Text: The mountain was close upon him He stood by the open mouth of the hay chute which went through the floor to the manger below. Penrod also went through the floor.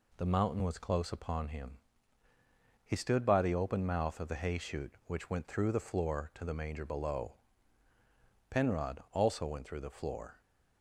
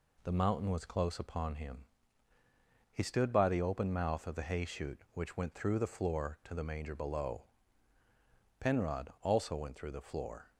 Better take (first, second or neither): neither